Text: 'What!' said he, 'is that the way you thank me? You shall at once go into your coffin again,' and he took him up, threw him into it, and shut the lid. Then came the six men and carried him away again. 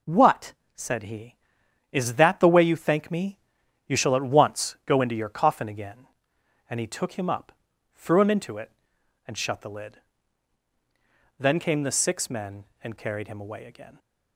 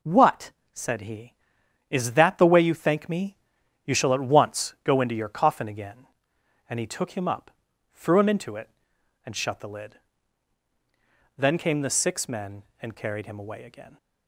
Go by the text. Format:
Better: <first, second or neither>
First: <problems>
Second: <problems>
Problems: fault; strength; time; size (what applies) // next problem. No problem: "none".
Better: neither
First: none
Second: none